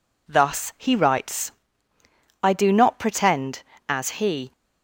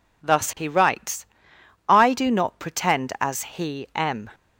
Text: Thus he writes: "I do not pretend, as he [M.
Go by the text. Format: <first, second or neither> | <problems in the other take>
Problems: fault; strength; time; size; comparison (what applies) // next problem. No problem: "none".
second | stops before "M"; at 4.5 s